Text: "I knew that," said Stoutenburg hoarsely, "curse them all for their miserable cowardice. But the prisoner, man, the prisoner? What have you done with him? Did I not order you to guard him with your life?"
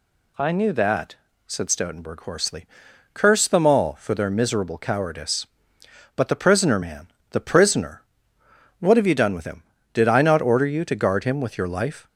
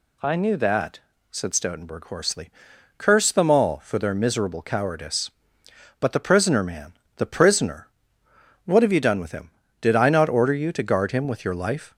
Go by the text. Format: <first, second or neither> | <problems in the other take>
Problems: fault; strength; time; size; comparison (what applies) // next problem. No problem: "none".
neither | none